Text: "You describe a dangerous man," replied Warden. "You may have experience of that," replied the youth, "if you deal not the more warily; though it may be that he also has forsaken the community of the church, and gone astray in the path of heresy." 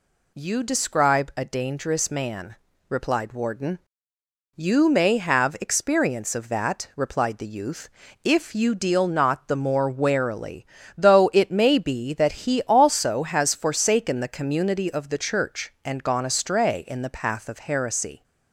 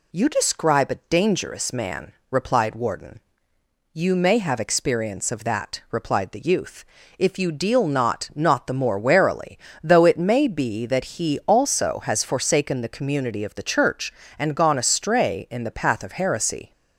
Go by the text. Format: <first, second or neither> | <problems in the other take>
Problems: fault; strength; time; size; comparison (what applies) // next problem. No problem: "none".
first | says "not" twice; at 8.3 s